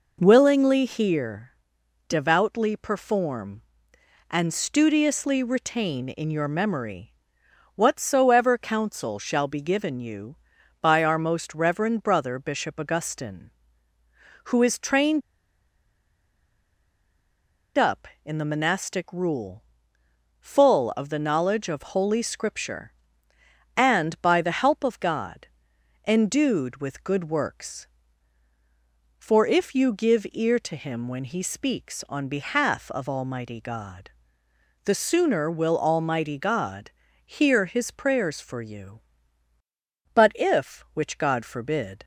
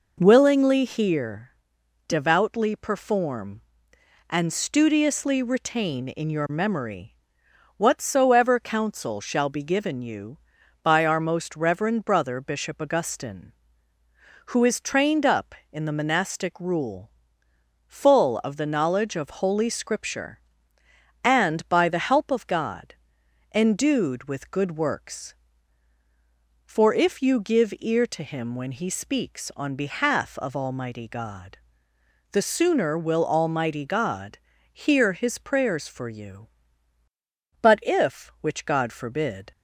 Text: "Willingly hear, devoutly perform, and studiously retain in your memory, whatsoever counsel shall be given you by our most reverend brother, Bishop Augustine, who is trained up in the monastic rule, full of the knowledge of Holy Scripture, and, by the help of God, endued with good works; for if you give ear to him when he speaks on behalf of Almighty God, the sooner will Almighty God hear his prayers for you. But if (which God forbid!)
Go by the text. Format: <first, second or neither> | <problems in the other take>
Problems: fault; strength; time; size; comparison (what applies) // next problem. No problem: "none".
second | pauses between "trained" and "up"; strong; at 15.2 s; 2.5 s long // pauses between "God" and "hear"; slight; at 36.8 s; 0.34 s long; slight in the second